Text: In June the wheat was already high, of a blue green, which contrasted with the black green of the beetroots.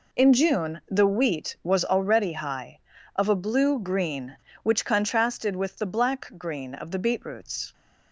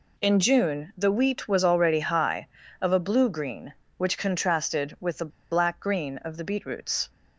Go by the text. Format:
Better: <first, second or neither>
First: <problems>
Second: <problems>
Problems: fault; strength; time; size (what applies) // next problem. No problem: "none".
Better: first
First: none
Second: pauses between "the" and "black"; slight; at 5.2 s; 0.22 s long